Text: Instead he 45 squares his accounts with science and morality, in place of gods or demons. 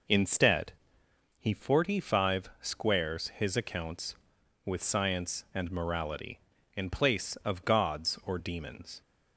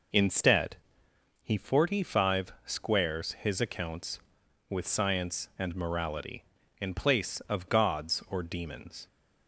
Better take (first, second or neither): neither